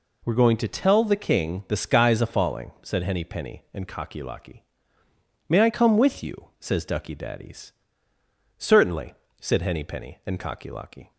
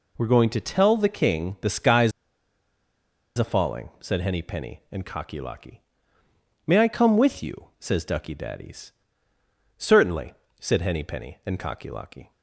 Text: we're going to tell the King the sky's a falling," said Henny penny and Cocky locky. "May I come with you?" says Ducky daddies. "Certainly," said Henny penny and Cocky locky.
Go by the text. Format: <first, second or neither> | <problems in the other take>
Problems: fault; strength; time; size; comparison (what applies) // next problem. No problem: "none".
first | pauses between "sky's" and "a"; strong; at 2.1 s; 1.2 s long